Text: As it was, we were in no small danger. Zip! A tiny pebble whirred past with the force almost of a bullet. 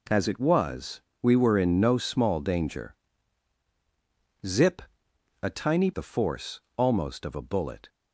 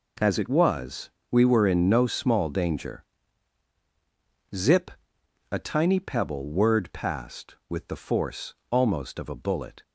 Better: second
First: skips "pebble whirred past with"; at 5.9 s // pauses between "force" and "almost"; slight; at 6.6 s; 0.16 s long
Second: pauses between "force" and "almost"; slight; at 8.5 s; 0.16 s long

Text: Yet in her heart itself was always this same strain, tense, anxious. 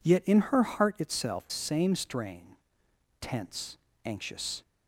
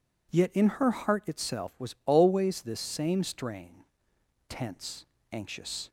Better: second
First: skips "was always this"; at 1.4 s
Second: none

